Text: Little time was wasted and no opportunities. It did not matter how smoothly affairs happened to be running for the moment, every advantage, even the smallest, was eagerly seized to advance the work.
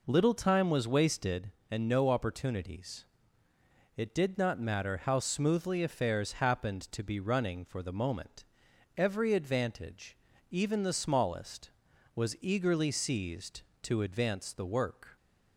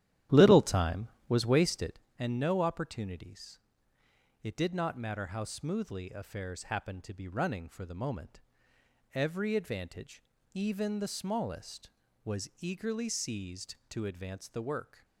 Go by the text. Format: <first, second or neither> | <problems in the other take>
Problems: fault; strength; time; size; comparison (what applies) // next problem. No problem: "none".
first | starts louder than the rest; strong; until 2.0 s; 12 dB